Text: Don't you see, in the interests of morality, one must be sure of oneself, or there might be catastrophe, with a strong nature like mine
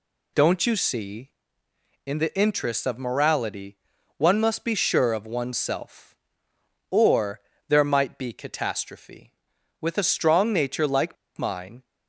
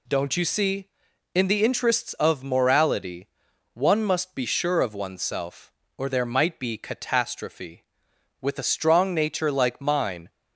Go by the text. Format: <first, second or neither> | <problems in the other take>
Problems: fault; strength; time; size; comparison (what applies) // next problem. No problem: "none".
second | pauses between "or" and "there"; slight; at 7.3 s; 0.28 s long // pauses between "like" and "mine"; slight; at 11.1 s; 0.22 s long